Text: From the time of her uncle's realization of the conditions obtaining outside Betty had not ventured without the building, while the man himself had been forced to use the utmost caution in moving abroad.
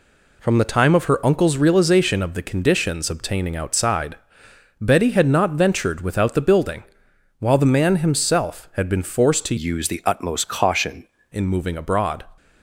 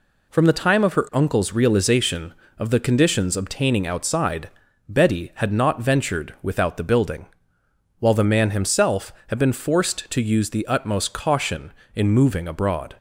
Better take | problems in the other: second | pauses between "outside" and "Betty"; noticeable; at 4.1 s; 0.64 s long; also in the second // changes voice from "use" to "caution"; from 9.5 to 11.0 s; 1.5 s long

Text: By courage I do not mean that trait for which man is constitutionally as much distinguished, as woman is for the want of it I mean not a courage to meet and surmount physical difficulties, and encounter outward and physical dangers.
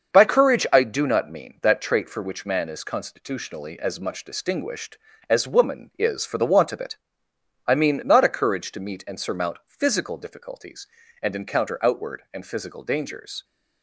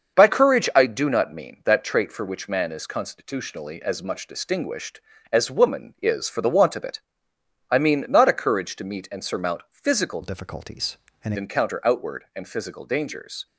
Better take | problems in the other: first | starts louder than the rest; until 1.2 s; 6.5 dB; also in the first // pauses between "it" and "I"; noticeable; at 6.9 s; 0.68 s long; noticeable in the first // changes voice from "difficulties" to "and"; from 10.2 to 11.3 s; 1.1 s long

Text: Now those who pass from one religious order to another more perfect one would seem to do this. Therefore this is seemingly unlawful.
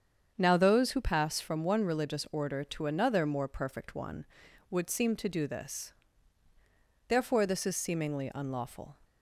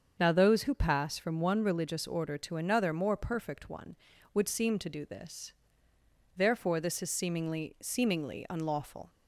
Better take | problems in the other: first | starts louder than the rest; until 1.2 s; 7 dB; strong in the first // says "seemingly" twice; at 7.8 s

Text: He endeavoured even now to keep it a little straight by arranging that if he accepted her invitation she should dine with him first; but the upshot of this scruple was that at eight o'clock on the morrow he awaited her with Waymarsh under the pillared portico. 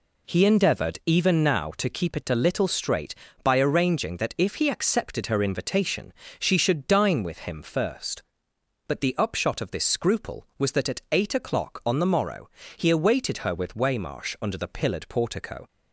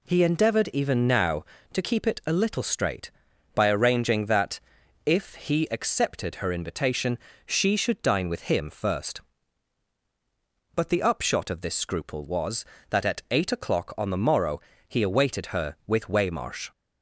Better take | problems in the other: first | pauses between "that" and "if"; noticeable; at 4.5 s; 0.46 s long // pauses between "invitation" and "she"; slight; at 7.1 s; 0.28 s long; slight in the first // pauses between "morrow" and "he"; slight; at 14.5 s; 0.30 s long; slight in the first // stops before "under the pillared portico"; at 16.7 s

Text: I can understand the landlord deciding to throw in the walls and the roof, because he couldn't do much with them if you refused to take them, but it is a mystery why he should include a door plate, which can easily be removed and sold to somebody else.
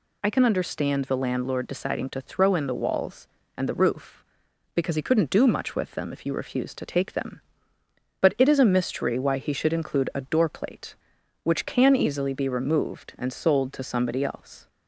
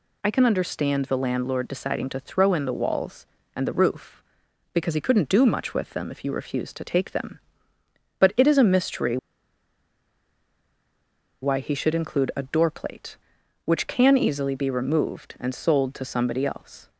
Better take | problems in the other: first | pauses between "mystery" and "why"; strong; at 9.1 s; 2.2 s long

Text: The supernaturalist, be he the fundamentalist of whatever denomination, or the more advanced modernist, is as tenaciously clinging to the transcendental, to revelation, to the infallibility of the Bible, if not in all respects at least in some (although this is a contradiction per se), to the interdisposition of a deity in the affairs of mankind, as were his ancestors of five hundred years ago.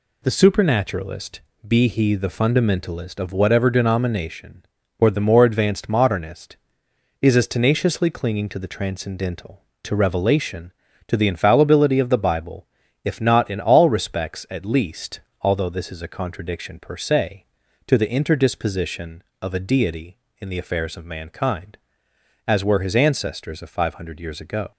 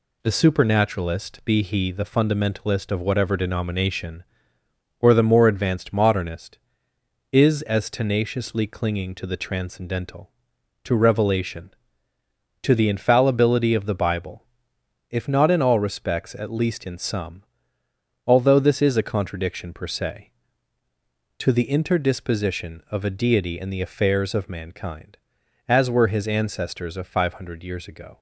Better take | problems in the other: second | skips "in some"; at 15.3 s

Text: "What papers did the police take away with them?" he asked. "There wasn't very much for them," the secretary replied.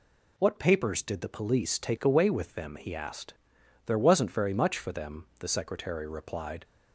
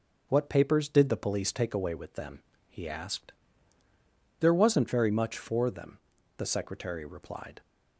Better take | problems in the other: neither | none

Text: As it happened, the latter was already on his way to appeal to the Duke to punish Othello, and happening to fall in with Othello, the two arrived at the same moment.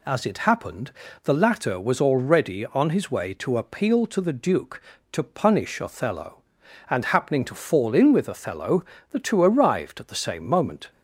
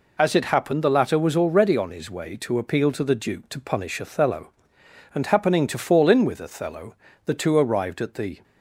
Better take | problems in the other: first | stops before "same moment"; at 8.4 s

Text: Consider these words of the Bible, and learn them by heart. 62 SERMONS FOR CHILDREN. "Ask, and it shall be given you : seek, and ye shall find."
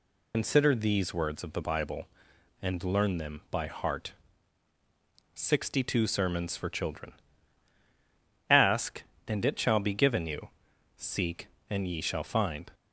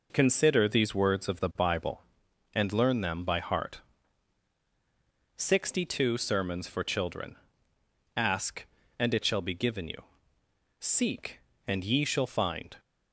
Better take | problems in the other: second | loses the start of "Consider"; at 0.3 s; 100 ms

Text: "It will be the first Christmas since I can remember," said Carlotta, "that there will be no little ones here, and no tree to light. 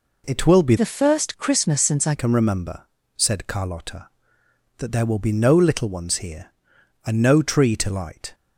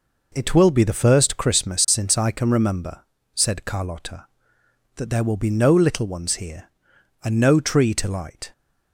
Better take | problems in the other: second | changes voice from "the" to "I"; from 0.7 to 2.1 s; 1.4 s long

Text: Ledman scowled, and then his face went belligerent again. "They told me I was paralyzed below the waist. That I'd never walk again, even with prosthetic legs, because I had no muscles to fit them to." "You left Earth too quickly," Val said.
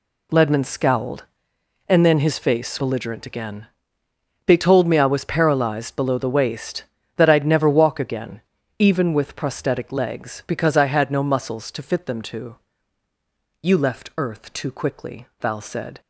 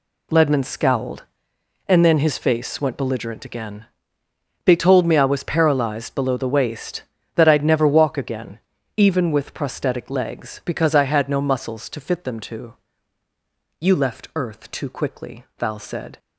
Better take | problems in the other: second | skips "went"; at 2.8 s

